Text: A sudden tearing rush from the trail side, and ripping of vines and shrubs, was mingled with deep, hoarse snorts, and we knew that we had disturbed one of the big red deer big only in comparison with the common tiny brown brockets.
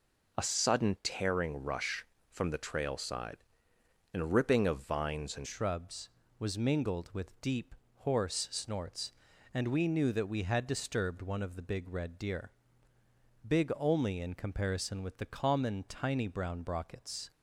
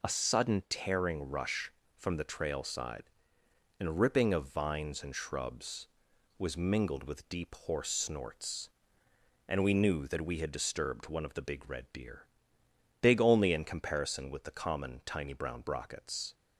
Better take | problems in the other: second | changes voice at "shrubs"; from 5.4 s on; 11.9 s long // pauses between "deer" and "big"; noticeable; at 12.5 s; 0.96 s long; noticeable in the second

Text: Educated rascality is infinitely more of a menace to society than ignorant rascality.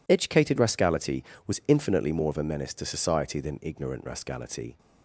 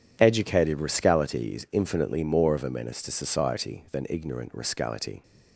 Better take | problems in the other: second | says "was" for "is"; at 1.4 s

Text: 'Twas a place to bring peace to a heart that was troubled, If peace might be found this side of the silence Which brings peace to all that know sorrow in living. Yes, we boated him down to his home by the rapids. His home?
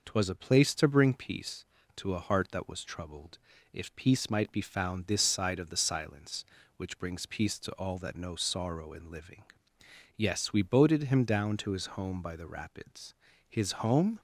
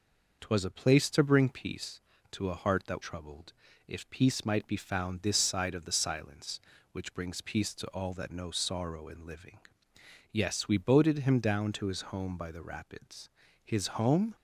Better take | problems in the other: first | skips "was"; at 3.0 s

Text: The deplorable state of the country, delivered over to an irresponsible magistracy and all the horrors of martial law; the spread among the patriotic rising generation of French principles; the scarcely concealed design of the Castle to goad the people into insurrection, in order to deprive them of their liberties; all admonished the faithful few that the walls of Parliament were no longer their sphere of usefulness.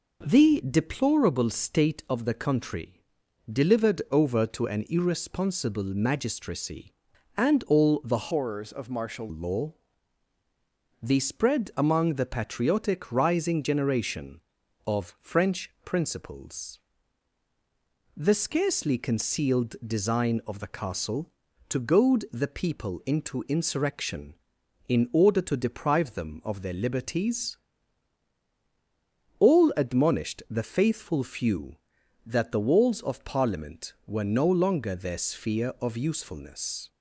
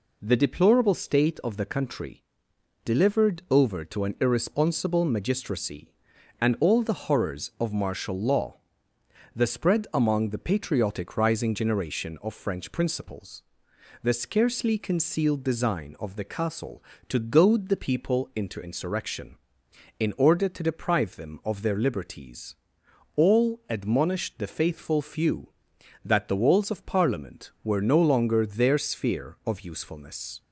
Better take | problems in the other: second | changes voice from "horrors" to "martial"; from 8.3 to 9.2 s; 0.9 s long

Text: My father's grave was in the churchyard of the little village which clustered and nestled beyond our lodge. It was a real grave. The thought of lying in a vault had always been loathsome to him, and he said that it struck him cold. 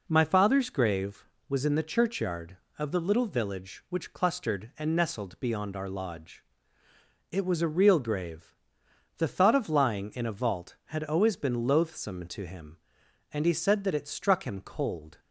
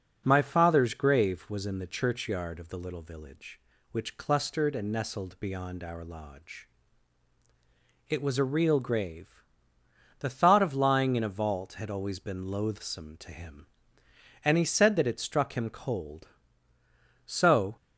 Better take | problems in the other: first | starts louder than the rest; noticeable; until 1.2 s; 6 dB // goes on to say "So"; from 17.2 s on; 0.50 s long

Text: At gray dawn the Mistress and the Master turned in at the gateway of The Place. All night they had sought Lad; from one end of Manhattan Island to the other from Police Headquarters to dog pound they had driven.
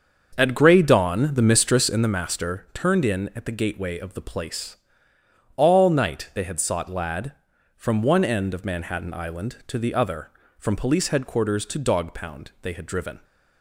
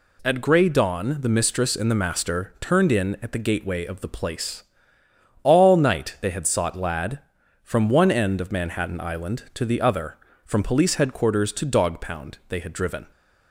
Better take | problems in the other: second | starts louder than the rest; until 2.2 s; 6.5 dB

